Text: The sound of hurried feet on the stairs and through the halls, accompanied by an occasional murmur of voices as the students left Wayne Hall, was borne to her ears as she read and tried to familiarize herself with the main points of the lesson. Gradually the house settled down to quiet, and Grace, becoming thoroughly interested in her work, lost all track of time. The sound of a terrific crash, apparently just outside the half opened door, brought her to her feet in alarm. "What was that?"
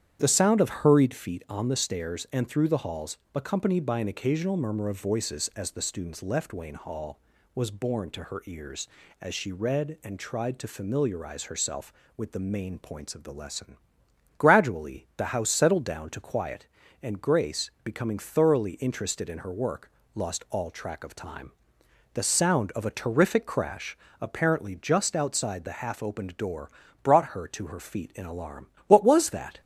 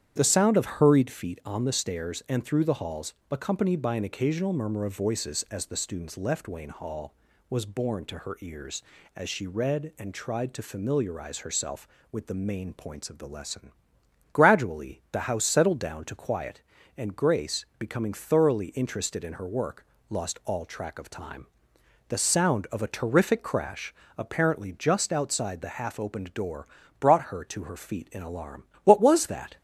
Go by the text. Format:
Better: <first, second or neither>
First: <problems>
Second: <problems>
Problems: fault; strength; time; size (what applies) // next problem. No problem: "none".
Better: neither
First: starts louder than the rest; strong; until 1.2 s; 9.5 dB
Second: starts louder than the rest; strong; until 1.1 s; 9.5 dB